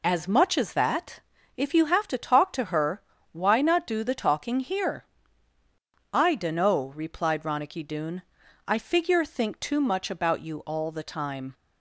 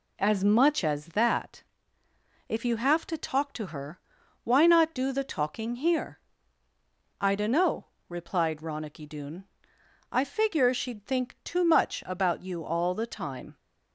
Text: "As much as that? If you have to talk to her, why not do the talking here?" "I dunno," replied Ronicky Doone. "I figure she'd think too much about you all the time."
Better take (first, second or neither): second